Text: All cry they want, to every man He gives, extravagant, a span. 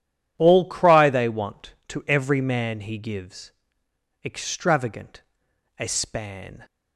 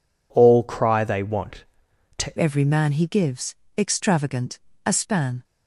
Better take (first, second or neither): first